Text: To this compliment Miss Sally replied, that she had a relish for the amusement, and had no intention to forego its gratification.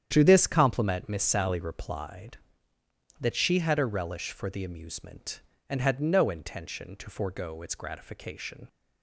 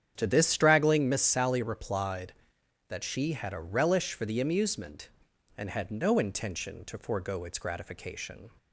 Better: first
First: starts louder than the rest; strong; until 1.1 s; 9 dB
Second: starts louder than the rest; strong; until 1.1 s; 8.5 dB // says "straggling" for "compliment"; at 0.4 s

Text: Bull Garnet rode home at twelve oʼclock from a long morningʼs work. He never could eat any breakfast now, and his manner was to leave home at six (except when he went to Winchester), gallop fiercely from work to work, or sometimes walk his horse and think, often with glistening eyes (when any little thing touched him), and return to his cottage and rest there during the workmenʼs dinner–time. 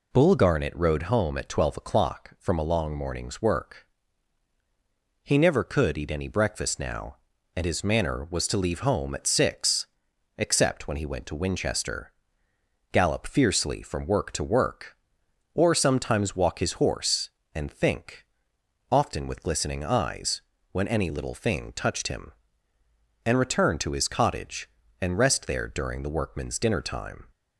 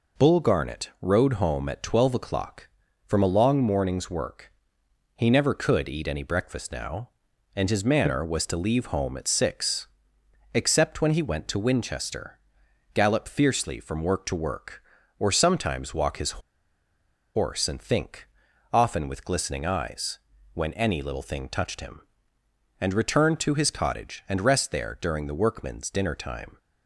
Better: first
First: none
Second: pauses between "his" and "horse"; at 16.3 s; 1.0 s long

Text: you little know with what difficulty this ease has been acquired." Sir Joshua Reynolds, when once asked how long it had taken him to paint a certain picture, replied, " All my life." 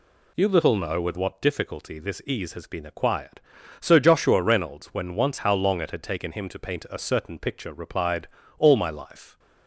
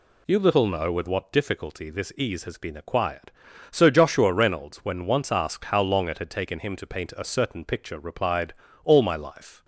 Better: second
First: skips "asked"; at 5.3 s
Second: none

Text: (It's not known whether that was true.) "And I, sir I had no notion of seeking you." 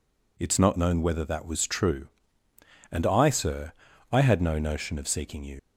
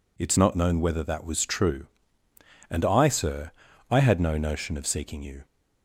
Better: second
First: pauses between "sir" and "I"; at 3.7 s; 0.40 s long // leaves "you" unfinished; at 5.5 s; 85 ms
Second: pauses between "sir" and "I"; at 3.5 s; 0.40 s long

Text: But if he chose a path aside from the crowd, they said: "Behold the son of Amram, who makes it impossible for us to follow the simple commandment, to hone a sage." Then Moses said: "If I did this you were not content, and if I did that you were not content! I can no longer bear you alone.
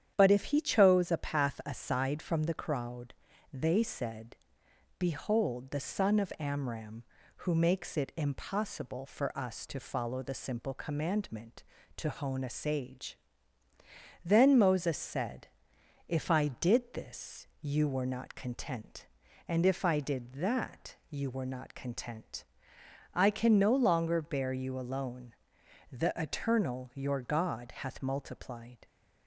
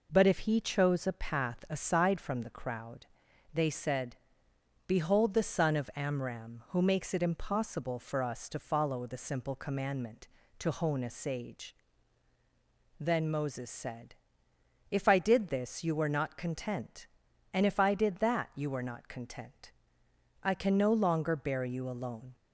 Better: second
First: starts louder than the rest; strong; until 1.1 s; 9.5 dB // pauses between "that" and "you"; slight; at 20.9 s; 0.16 s long // goes on to say "The Eternal your God hath multiplied"; strong; from 25.8 s on; 2.9 s long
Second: none

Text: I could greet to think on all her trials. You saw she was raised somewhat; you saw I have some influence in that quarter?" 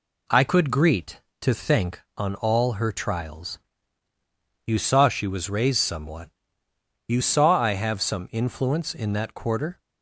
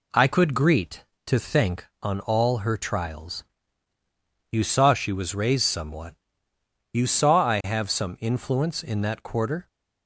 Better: neither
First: none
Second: none

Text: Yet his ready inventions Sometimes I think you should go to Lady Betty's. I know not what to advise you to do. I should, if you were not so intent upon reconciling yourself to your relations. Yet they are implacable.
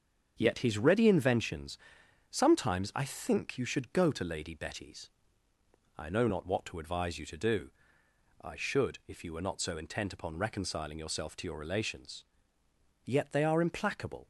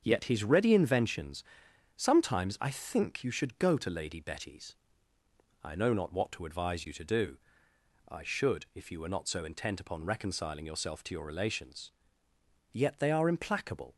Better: neither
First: starts louder than the rest; until 1.3 s; 7 dB // pauses between "inventions" and "Sometimes"; noticeable; at 1.7 s; 0.52 s long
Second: starts louder than the rest; until 1.0 s; 7 dB // pauses between "inventions" and "Sometimes"; noticeable; at 1.4 s; 0.52 s long

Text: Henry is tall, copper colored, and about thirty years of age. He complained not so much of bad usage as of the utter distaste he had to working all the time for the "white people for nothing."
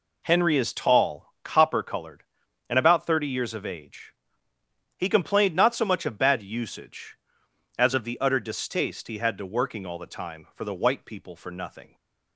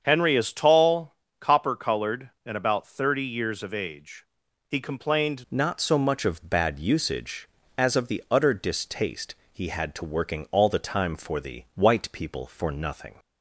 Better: first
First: none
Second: starts louder than the rest; strong; until 1.0 s; 7.5 dB // changes voice at "not"; from 5.4 s on; 7.7 s long // pauses between "distaste" and "he"; slight; at 9.3 s; 0.18 s long

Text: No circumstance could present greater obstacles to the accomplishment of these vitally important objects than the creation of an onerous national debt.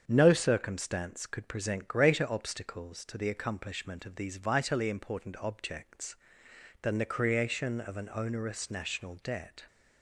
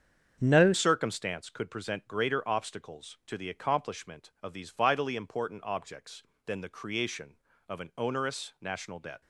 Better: first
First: starts louder than the rest; strong; until 1.0 s; 7.5 dB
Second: starts louder than the rest; strong; until 1.4 s; 7.5 dB // changes voice at "circumstance"; from 0.7 s on; 8.5 s long

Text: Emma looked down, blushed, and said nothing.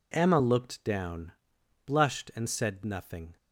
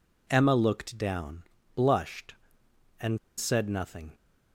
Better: first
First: none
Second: pauses between "and" and "said"; slight; at 3.1 s; 0.21 s long

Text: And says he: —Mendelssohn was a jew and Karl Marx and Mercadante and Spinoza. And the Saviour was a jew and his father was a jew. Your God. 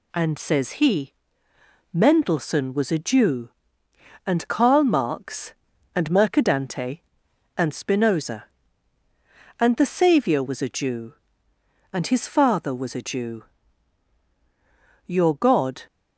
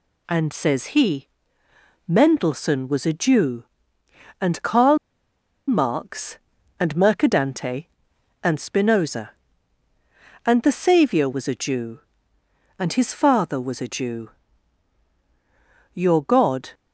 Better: first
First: none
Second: pauses between "Karl" and "Marx"; noticeable; at 4.9 s; 0.70 s long

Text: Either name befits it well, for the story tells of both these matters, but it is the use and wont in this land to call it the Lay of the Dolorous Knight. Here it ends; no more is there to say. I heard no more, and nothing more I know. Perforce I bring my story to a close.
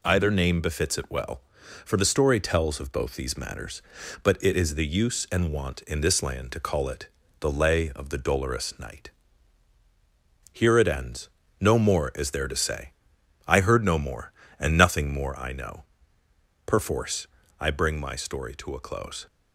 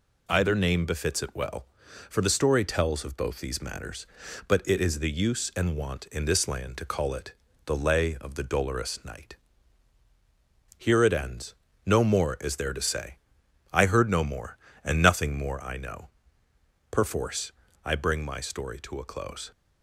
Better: neither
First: pauses between "it" and "the"; slight; at 7.0 s; 0.32 s long // pauses between "Perforce" and "I"; slight; at 17.2 s; 0.34 s long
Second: pauses between "it" and "the"; slight; at 7.3 s; 0.32 s long // pauses between "Perforce" and "I"; slight; at 17.5 s; 0.34 s long

